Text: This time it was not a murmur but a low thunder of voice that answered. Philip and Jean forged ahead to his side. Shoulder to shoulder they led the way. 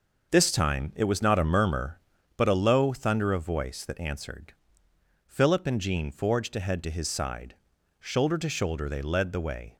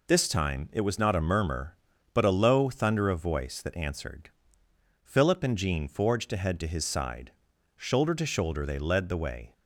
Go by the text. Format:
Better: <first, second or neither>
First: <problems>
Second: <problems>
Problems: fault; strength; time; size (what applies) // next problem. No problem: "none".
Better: second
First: starts louder than the rest; until 2.2 s; 6 dB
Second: none